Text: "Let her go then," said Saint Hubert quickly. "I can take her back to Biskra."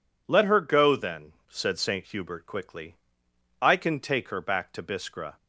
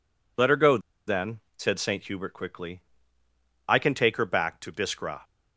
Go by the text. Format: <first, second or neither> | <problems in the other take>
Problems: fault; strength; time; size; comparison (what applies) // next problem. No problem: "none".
first | pauses between "go" and "then"; slight; at 0.7 s; 0.28 s long